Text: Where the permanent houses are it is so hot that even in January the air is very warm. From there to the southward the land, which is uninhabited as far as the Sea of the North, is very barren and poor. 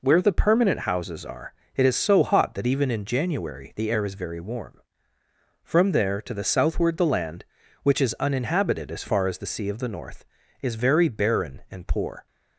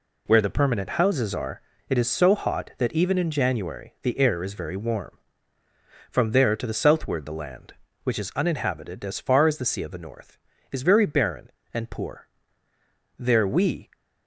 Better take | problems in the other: first | pauses between "are" and "it"; slight; at 1.6 s; 0.28 s long; slight in the first // goes on to say "There we"; noticeable; from 13.1 s on; 0.72 s long

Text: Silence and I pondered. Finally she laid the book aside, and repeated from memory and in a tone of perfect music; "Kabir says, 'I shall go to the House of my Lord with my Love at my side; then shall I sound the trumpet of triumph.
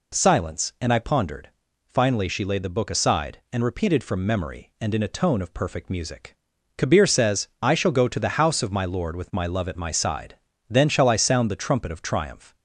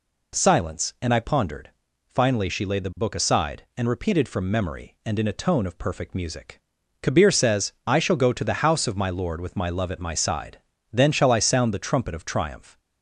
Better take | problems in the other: neither | none

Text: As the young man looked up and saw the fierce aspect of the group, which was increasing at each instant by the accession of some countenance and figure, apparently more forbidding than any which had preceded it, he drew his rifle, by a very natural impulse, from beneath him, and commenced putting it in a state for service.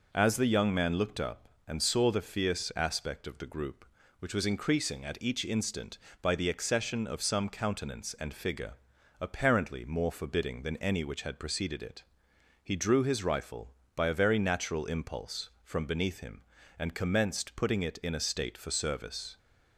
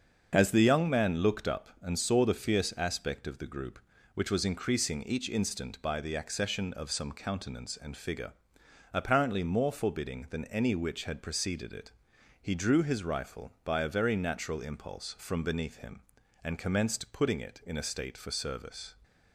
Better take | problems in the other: first | starts louder than the rest; until 1.3 s; 7 dB // skips "at"; at 5.0 s

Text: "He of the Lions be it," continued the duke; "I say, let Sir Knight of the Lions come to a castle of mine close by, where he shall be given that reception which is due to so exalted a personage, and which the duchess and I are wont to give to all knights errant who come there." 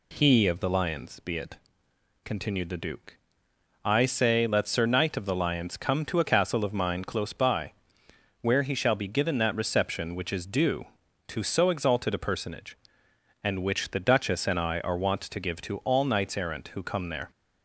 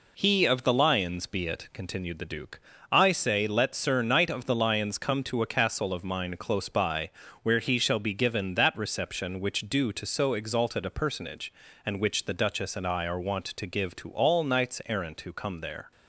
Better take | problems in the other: first | skips "is"; at 9.6 s

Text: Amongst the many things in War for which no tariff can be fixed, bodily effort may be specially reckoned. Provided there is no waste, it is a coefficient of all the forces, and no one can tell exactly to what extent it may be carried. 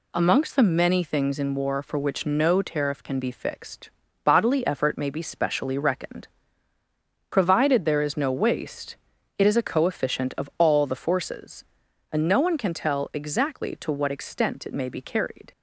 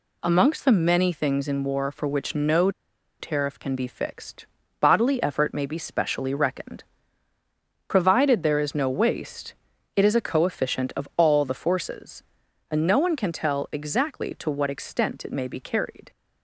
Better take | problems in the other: first | pauses between "no" and "tariff"; noticeable; at 2.7 s; 0.48 s long

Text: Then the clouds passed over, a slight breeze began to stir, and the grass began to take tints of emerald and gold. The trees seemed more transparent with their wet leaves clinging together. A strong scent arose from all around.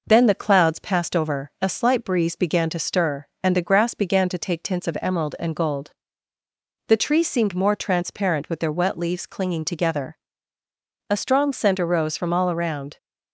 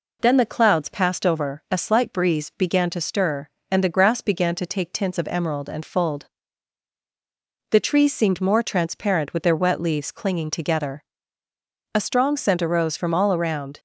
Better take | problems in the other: first | says "fold" for "gold"; at 5.8 s

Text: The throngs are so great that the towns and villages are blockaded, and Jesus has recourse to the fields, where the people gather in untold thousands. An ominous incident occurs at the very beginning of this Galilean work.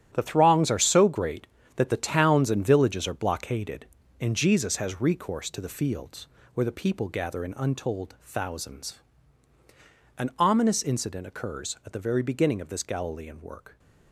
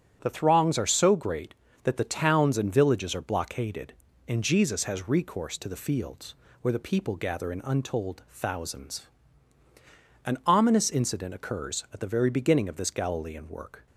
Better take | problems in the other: second | gets quieter; strong; throughout; 10.5 dB // starts louder than the rest; strong; until 1.1 s; 11 dB; strong in the second

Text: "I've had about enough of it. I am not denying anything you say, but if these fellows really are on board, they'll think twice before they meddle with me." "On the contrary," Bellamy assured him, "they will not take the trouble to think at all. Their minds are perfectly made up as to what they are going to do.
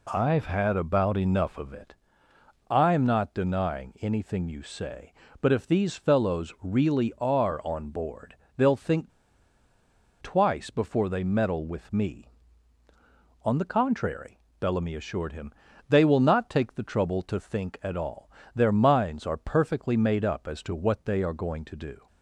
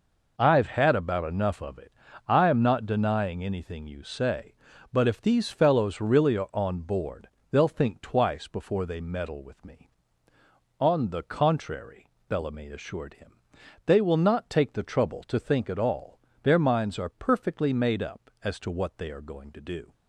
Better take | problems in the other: second | pauses between "think" and "twice"; at 9.1 s; 1.1 s long

